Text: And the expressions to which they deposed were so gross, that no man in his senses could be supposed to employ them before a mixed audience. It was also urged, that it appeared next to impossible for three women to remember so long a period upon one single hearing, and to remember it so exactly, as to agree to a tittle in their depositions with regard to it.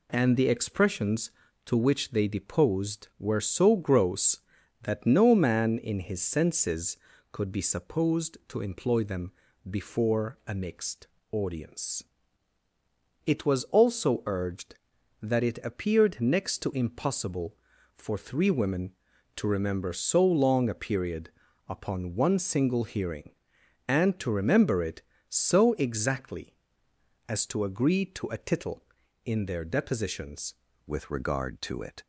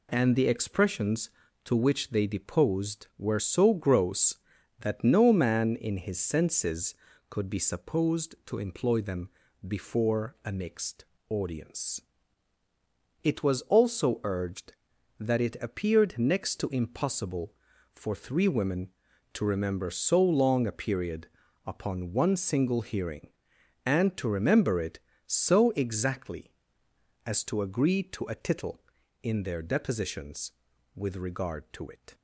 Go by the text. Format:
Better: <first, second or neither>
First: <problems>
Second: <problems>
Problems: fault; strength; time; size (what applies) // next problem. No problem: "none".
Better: second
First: pauses between "them" and "before"; at 9.3 s; 0.38 s long // pauses between "mixed" and "audience"; slight; at 11.0 s; 0.24 s long // pauses between "period" and "upon"; at 21.2 s; 0.40 s long // changes voice at "with"; from 30.8 s on; 1.2 s long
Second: pauses between "them" and "before"; at 9.2 s; 0.38 s long // pauses between "mixed" and "audience"; slight; at 11.0 s; 0.24 s long // pauses between "period" and "upon"; at 21.2 s; 0.40 s long